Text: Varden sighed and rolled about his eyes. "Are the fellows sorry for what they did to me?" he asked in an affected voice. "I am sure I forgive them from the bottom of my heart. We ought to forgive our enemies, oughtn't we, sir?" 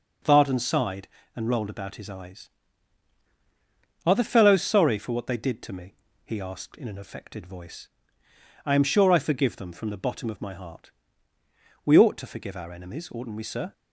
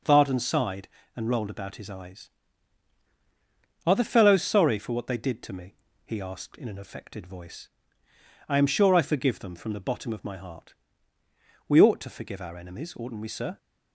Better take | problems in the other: neither | none

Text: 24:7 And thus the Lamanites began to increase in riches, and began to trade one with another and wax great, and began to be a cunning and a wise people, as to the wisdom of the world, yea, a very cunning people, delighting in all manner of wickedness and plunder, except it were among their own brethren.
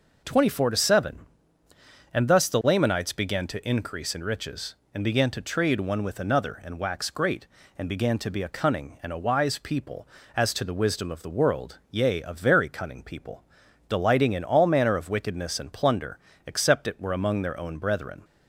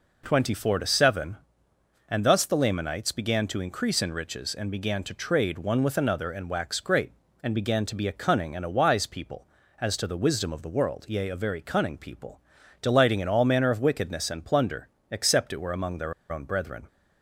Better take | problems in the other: first | pauses between "their" and "own"; slight; at 16.1 s; 0.17 s long

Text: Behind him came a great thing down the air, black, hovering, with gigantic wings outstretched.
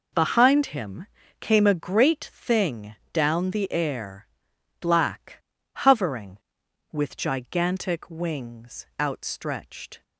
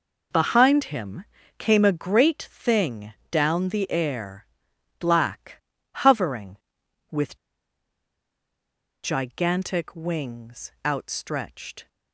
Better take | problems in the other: first | pauses between "him" and "came"; slight; at 1.2 s; 0.34 s long; slight in the first // pauses between "thing" and "down"; slight; at 3.1 s; 0.18 s long; slight in the first // pauses between "with" and "gigantic"; strong; at 7.3 s; 1.6 s long // pauses between "wings" and "outstretched"; slight; at 10.6 s; 0.16 s long; slight in the first

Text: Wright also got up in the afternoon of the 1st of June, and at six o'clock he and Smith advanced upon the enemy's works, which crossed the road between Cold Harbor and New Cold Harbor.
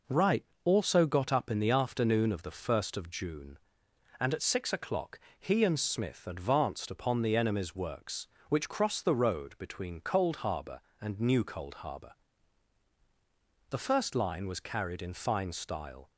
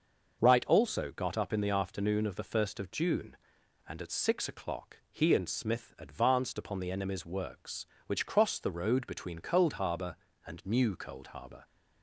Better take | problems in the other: second | pauses between "Wright" and "also"; slight; at 0.4 s; 0.20 s long // pauses between "o'clock" and "he"; slight; at 5.1 s; 0.20 s long // goes on to say "The first line was carried in fine style"; strong; from 13.7 s on; 2.4 s long

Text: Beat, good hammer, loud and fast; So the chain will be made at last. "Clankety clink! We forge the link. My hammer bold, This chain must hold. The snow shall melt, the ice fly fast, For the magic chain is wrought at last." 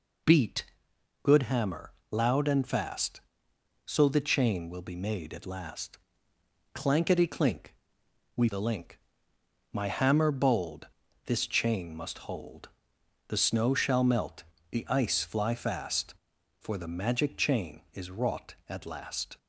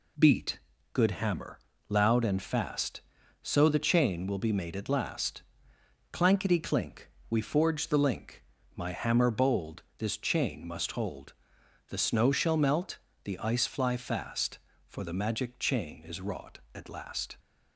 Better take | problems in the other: second | skips "forge"; at 8.4 s

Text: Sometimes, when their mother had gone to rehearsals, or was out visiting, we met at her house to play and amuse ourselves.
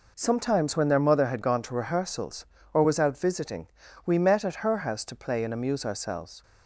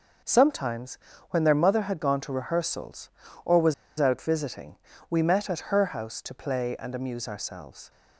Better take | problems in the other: first | pauses between "was" and "out"; slight; at 3.7 s; 0.25 s long

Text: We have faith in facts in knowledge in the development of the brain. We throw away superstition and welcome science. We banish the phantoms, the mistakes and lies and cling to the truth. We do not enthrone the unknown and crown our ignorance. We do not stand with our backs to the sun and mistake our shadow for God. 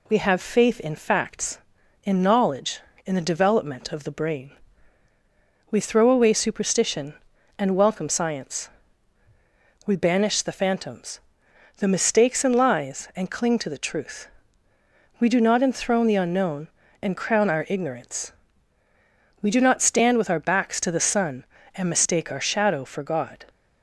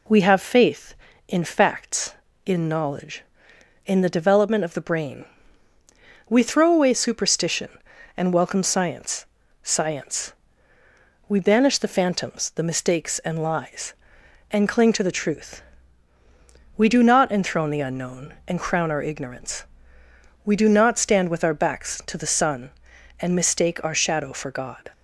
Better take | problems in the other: first | says "science" twice; at 9.6 s

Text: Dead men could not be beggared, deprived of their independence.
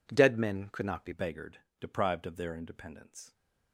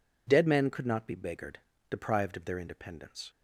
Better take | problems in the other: second | changes voice at "beggared"; from 1.1 s on; 2.2 s long

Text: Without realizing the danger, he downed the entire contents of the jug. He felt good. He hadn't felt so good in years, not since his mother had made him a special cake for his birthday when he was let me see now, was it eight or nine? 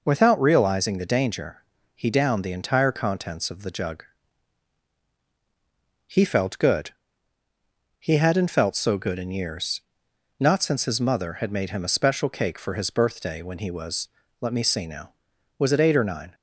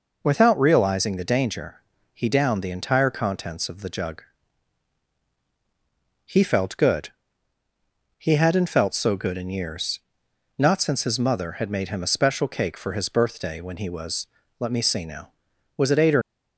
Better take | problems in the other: first | pauses between "was" and "let"; slight; at 14.2 s; 0.32 s long; slight in the first // stops before "nine"; at 16.2 s

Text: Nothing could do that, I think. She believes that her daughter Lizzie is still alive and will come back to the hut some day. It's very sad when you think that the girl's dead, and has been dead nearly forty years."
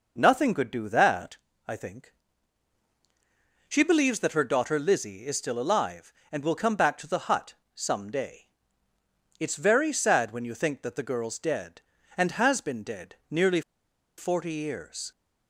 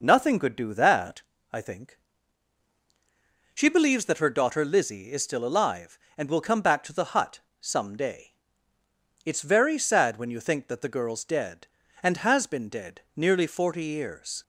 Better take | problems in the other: second | pauses between "hut" and "some"; slight; at 7.5 s; 0.22 s long; slight in the second // pauses between "nearly" and "forty"; noticeable; at 13.6 s; 0.57 s long

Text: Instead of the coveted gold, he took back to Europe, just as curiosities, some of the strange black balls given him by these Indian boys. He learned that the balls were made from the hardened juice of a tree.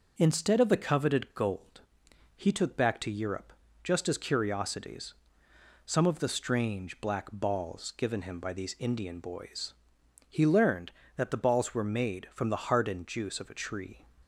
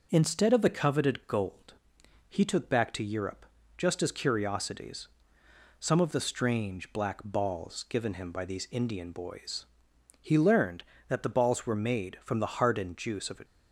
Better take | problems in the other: first | stops before "tree"; at 13.4 s

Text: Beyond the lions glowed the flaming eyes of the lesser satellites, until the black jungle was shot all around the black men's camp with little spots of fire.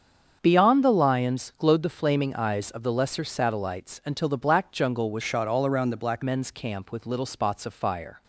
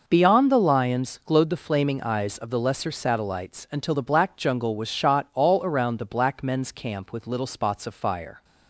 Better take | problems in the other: second | starts louder than the rest; strong; until 1.4 s; 7.5 dB // changes voice from "shot" to "black"; from 5.2 to 6.2 s; 1.0 s long

